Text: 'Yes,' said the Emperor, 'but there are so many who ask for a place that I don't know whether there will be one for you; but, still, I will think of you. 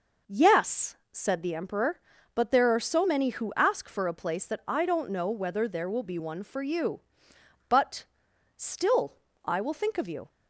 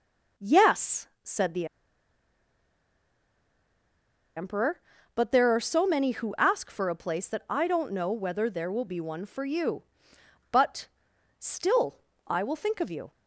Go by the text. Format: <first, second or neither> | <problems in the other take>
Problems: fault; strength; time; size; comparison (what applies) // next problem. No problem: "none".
first | pauses between "the" and "Emperor"; strong; at 1.6 s; 2.6 s long